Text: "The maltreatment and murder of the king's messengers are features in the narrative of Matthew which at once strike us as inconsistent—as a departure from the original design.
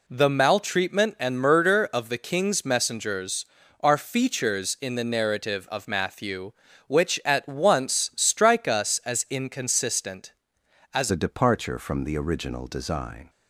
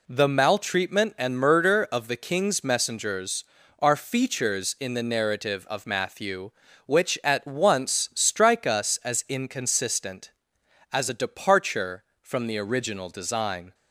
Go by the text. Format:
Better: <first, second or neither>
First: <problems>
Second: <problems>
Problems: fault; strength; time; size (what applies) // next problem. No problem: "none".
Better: second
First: changes voice at "a"; from 11.1 s on; 2.1 s long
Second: none